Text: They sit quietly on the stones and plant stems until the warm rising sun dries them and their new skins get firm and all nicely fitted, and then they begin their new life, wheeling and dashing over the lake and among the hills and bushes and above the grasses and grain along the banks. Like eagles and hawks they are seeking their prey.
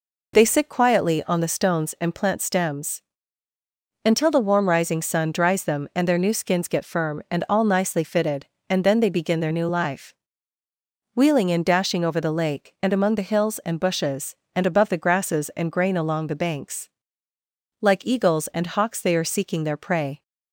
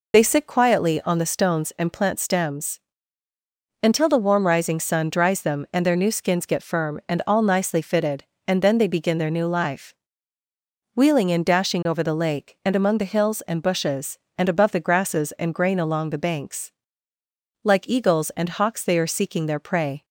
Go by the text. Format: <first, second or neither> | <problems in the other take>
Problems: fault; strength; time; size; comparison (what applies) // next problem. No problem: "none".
first | loses the start of "They"; at 0.1 s; 30 ms // pauses between "stems" and "until"; at 2.8 s; 1.0 s long; also in the first